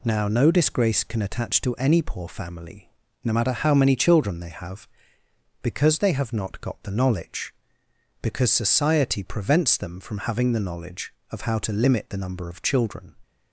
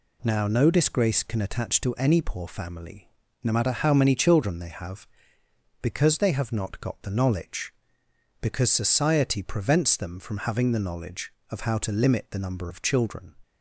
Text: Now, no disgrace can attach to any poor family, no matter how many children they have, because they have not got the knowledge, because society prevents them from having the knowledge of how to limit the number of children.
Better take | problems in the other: neither | none

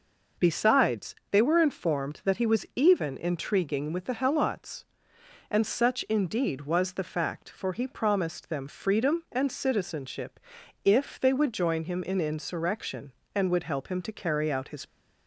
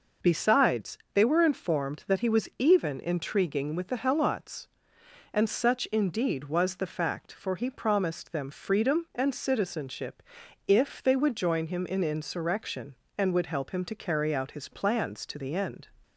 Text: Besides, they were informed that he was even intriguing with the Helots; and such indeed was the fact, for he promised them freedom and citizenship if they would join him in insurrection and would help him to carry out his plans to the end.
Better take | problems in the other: second | pauses between "citizenship" and "if"; noticeable; at 10.3 s; 0.46 s long; noticeable in the second // stops before "plans to the end"; at 14.8 s

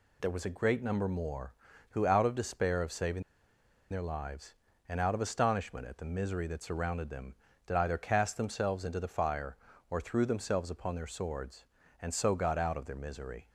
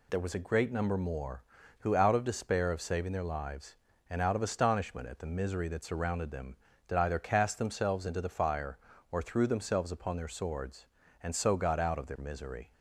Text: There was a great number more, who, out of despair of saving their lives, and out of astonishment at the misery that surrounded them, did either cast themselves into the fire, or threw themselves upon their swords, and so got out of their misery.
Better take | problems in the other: second | pauses between "saving" and "their"; noticeable; at 3.2 s; 0.68 s long

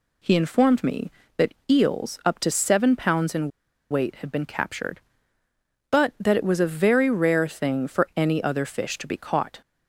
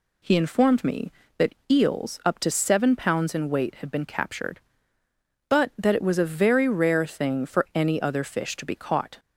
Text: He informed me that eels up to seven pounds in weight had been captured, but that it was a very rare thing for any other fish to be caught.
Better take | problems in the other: second | pauses between "that" and "eels"; slight; at 1.5 s; 0.16 s long; slight in the second // pauses between "in" and "weight"; at 3.4 s; 0.42 s long

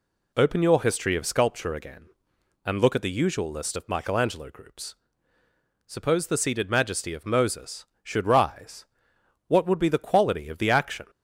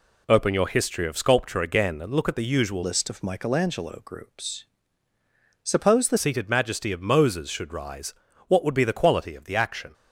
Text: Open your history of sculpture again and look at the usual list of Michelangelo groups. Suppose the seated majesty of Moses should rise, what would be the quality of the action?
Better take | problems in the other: first | changes voice from "list" to "the"; from 2.8 to 6.1 s; 3.3 s long

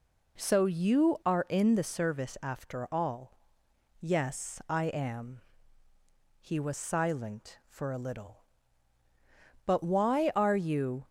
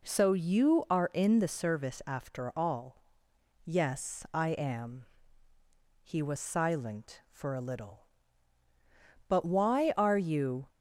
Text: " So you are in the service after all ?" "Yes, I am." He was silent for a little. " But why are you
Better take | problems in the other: neither | none

